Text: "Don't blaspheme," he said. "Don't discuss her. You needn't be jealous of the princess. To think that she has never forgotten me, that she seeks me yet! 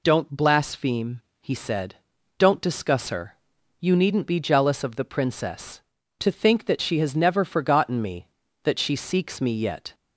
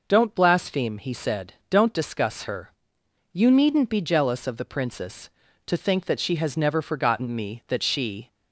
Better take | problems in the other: first | stops before "seeks me yet"; at 8.3 s

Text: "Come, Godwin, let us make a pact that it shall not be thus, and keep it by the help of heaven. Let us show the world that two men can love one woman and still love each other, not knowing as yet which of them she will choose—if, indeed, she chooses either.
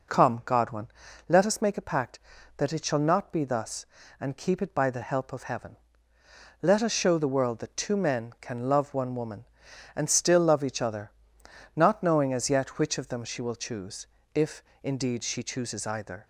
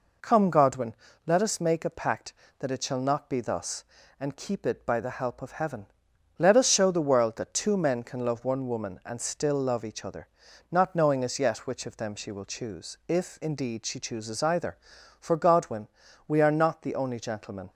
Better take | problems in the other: first | goes on to say "For Godwin we are not the only gentlemen"; strong; from 15.2 s on; 2.5 s long

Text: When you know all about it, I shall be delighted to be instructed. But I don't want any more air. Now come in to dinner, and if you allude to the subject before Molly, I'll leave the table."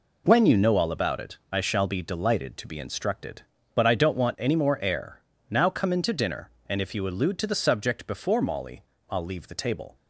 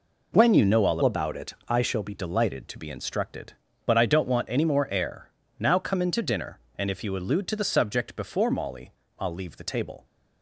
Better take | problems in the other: first | changes voice from "about" to "be"; from 1.0 to 2.1 s; 1.1 s long

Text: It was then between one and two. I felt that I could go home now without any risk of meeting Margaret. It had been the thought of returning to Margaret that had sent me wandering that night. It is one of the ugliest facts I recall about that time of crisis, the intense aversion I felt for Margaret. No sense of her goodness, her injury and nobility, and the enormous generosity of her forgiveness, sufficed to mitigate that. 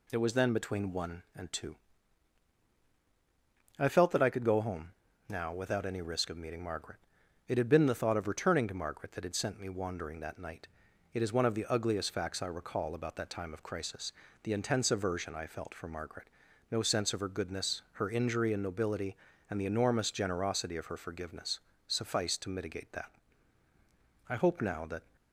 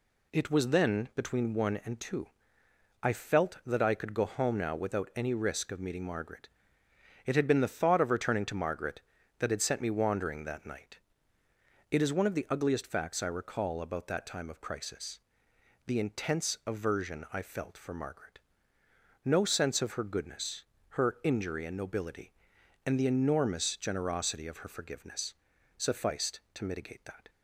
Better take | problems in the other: second | pauses between "home" and "now"; at 4.9 s; 0.38 s long // goes on to say "I hope now that"; noticeable; from 24.2 s on; 0.88 s long

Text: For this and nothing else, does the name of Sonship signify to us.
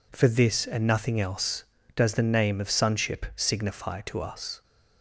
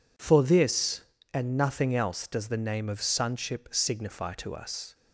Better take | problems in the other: neither | none

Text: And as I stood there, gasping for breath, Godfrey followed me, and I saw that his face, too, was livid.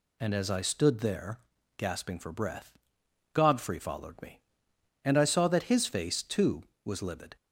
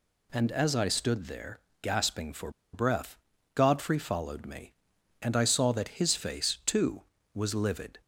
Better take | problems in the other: first | pauses between "for" and "breath"; slight; at 2.5 s; 0.22 s long

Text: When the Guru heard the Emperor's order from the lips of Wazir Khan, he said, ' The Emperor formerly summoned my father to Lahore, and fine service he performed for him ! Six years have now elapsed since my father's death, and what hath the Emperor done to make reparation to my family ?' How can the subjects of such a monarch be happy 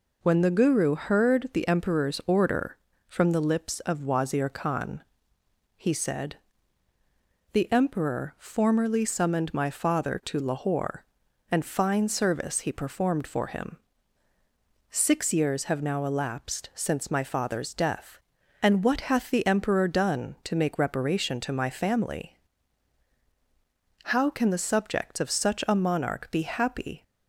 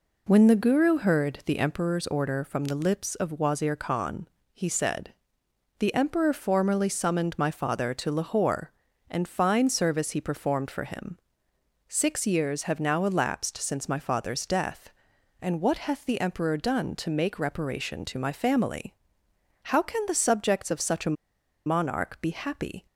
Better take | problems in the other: first | pauses between "a" and "monarch"; noticeable; at 21.1 s; 0.50 s long

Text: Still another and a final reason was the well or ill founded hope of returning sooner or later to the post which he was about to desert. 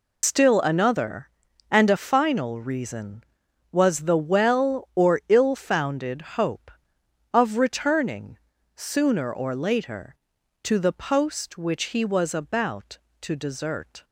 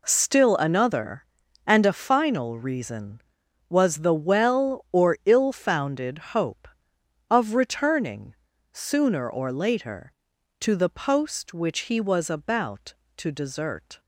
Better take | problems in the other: second | loses the start of "Still"; at 0.2 s; 145 ms // pauses between "founded" and "hope"; slight; at 6.2 s; 0.16 s long; slight in the second // pauses between "returning" and "sooner"; at 8.3 s; 0.40 s long; also in the second

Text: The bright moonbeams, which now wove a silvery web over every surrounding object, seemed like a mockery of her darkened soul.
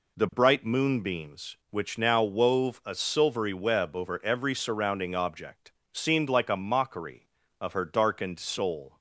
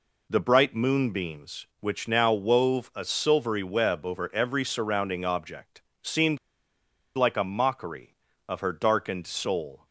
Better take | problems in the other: first | pauses between "seemed" and "like"; noticeable; at 6.3 s; 0.77 s long

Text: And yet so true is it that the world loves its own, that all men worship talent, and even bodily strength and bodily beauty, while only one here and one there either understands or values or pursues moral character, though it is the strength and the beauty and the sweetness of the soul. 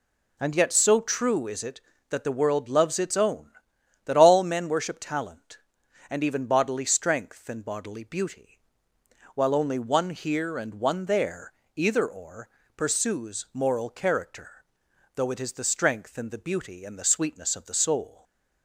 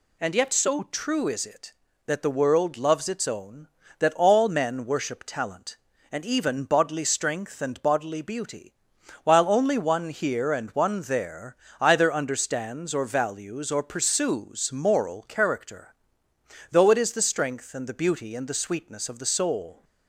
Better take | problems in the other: second | pauses between "there" and "either"; slight; at 11.5 s; 0.22 s long; slight in the second // skips "understands or values"; at 12.0 s // pauses between "or" and "pursues"; slight; at 12.4 s; 0.28 s long // stays silent after the last word; slight; from 18.0 s on; 0.6 s long

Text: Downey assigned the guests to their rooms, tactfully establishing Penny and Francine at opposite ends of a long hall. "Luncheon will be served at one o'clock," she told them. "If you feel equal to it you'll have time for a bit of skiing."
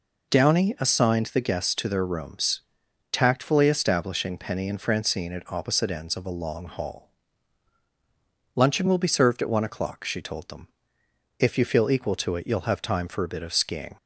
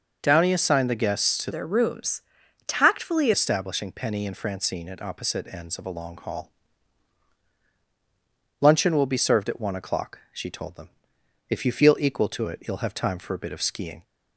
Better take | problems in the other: first | changes voice from "their" to "tactfully"; from 1.5 to 3.3 s; 1.8 s long

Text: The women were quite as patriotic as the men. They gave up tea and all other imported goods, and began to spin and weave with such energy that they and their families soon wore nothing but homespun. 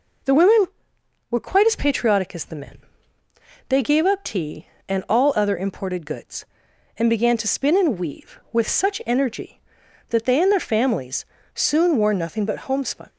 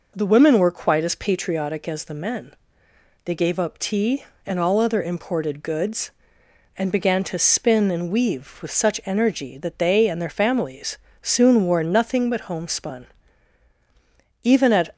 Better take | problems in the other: first | pauses between "families" and "soon"; slight; at 10.9 s; 0.24 s long; slight in the first // goes on to say "Even at"; from 14.4 s on; 0.50 s long

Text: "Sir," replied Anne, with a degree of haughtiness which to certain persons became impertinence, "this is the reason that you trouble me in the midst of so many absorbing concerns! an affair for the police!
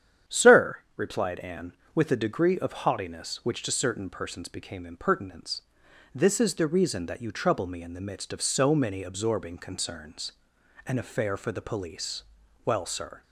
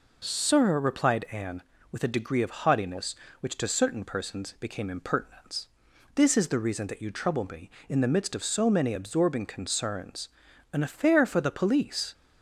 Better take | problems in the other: second | starts louder than the rest; strong; until 1.4 s; 9.5 dB // goes on to say "Well sir"; from 12.6 s on; 0.58 s long

